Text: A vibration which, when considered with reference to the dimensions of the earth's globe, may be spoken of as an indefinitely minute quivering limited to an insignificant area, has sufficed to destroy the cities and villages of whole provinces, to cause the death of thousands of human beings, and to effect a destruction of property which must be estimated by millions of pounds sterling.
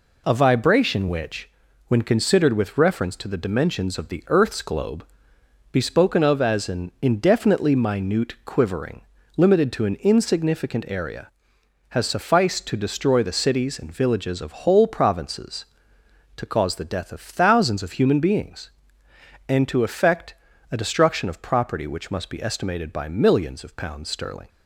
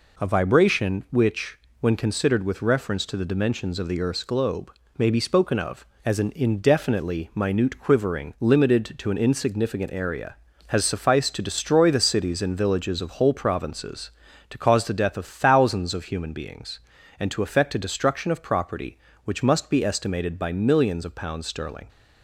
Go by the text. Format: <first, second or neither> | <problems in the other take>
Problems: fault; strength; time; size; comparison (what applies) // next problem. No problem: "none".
second | skips "may"; at 5.3 s // pauses between "quivering" and "limited"; slight; at 9.0 s; 0.34 s long // pauses between "effect" and "a"; at 20.3 s; 0.38 s long